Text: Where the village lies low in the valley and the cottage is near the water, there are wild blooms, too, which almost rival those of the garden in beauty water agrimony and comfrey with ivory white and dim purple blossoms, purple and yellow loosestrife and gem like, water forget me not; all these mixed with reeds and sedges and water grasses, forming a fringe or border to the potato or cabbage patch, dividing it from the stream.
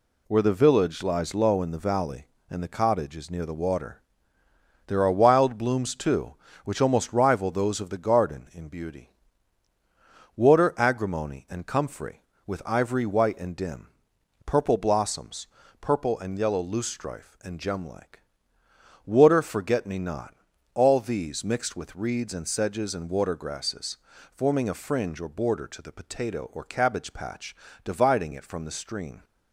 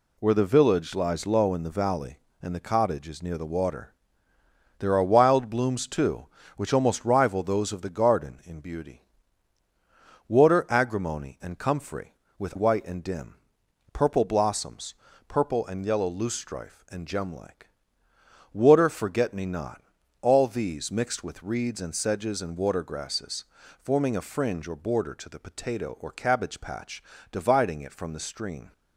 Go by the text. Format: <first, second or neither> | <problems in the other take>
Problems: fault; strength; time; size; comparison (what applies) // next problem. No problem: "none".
first | pauses between "beauty" and "water"; strong; at 9.0 s; 1.2 s long; strong in the first // skips "ivory"; at 12.5 s // pauses between "dim" and "purple"; noticeable; at 13.3 s; 0.58 s long; noticeable in the first